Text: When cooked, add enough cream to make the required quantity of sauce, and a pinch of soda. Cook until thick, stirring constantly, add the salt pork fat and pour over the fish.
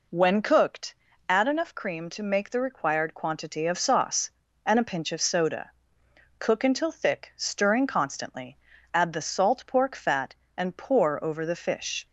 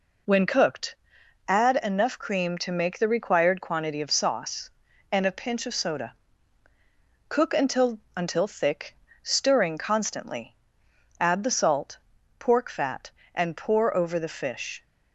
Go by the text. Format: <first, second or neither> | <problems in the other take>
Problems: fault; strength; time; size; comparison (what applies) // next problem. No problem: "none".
first | says "until" twice; at 8.1 s // pauses between "salt" and "pork"; at 11.9 s; 0.40 s long